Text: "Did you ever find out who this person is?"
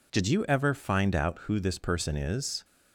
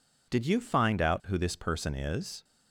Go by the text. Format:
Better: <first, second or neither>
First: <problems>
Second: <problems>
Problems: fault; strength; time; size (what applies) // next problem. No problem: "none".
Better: first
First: none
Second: skips "ever"; at 0.6 s